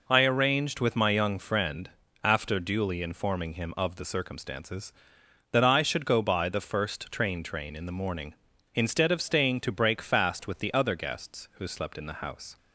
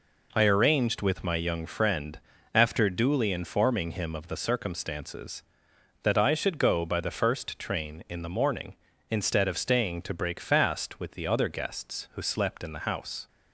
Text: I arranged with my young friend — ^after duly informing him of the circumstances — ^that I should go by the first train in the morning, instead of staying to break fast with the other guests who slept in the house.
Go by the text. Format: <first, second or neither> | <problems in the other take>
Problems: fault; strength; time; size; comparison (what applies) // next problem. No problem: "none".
second | says "train" twice; at 7.4 s